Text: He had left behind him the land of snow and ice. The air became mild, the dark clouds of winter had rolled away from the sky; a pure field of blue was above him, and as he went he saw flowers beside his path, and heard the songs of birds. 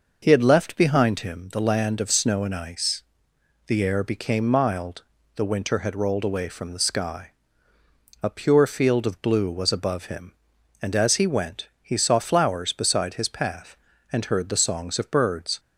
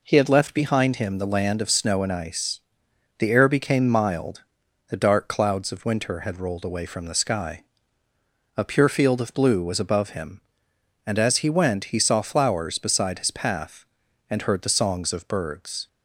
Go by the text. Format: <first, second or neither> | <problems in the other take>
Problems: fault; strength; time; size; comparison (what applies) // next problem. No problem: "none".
second | skips "dark clouds of"; at 5.4 s